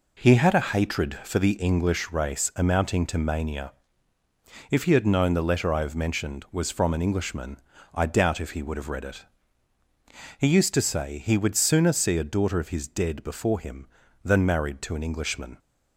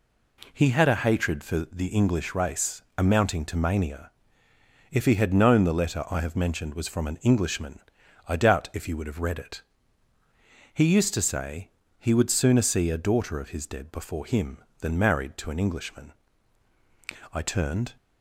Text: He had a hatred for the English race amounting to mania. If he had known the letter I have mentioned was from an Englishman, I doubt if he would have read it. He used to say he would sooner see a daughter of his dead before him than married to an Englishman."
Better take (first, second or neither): first